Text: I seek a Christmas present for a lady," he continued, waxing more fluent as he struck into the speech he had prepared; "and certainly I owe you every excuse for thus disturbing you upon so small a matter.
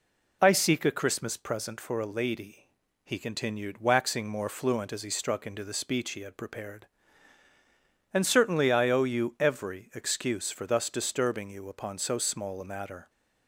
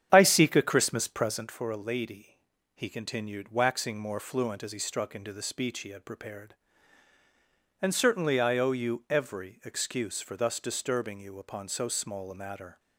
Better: first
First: none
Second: starts louder than the rest; strong; until 1.6 s; 9 dB

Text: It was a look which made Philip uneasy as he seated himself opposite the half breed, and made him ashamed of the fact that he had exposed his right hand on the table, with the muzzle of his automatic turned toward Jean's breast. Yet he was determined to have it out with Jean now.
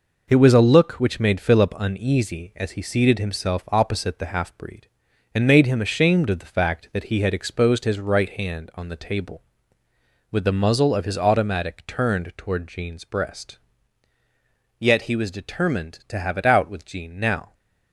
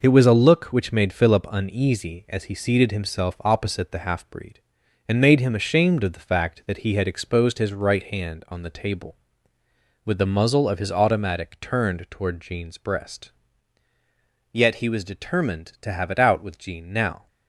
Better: neither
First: none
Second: none

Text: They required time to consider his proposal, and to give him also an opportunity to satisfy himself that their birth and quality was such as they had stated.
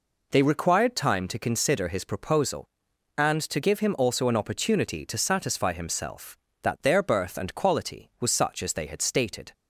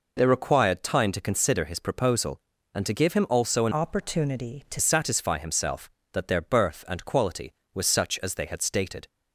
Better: first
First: none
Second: changes voice from "opportunity" to "to"; from 3.7 to 4.7 s; 1.0 s long

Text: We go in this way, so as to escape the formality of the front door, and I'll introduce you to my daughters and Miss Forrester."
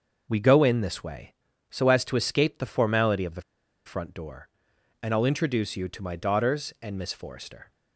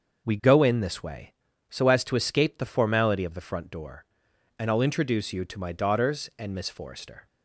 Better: second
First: starts louder than the rest; until 1.3 s; 6 dB // pauses between "the" and "front"; at 3.4 s; 0.44 s long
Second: starts louder than the rest; noticeable; until 1.3 s; 6 dB

